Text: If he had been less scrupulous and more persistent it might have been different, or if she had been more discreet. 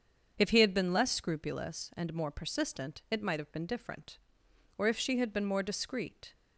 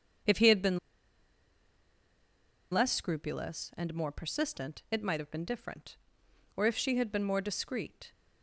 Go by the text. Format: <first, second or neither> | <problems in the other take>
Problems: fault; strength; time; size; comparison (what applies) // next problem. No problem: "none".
first | starts louder than the rest; until 3.1 s; 7 dB; also in the first // pauses between "been" and "less"; strong; at 0.7 s; 1.9 s long